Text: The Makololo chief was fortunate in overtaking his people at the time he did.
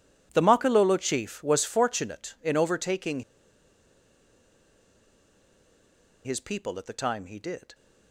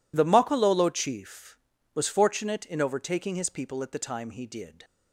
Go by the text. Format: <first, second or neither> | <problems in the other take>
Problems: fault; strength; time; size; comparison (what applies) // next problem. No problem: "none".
second | pauses between "overtaking" and "his"; strong; at 3.2 s; 3.0 s long